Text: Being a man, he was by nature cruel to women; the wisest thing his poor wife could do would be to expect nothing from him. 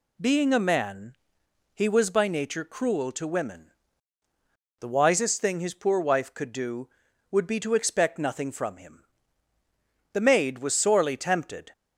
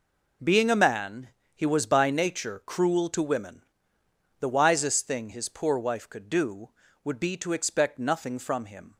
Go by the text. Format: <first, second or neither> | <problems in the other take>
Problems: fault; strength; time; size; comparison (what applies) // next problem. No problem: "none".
second | goes on to say "The maid was sorely tempted"; from 10.1 s on; 1.6 s long